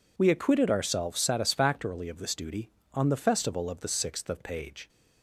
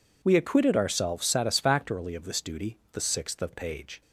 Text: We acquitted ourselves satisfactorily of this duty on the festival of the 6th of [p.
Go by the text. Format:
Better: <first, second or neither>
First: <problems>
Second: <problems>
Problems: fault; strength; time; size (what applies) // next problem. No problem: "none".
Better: first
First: none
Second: skips "on the festival of"; at 2.8 s